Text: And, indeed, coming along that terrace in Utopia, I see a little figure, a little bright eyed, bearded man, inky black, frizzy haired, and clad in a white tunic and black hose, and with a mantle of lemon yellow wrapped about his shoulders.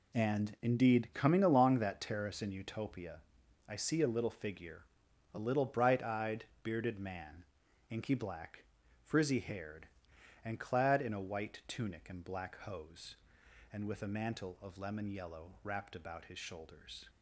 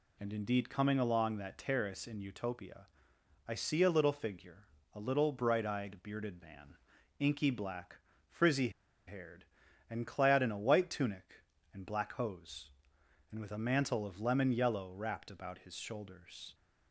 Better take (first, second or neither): first